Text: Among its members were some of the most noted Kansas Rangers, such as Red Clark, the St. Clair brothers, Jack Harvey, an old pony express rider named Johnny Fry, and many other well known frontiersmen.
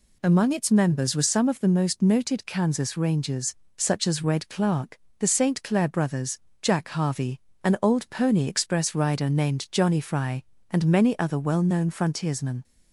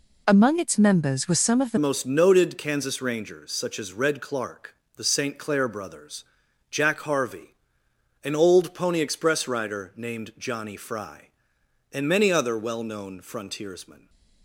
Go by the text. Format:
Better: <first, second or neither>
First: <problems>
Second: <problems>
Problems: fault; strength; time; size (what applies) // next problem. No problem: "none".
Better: first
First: none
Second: changes voice at "most"; from 1.7 s on; 12.3 s long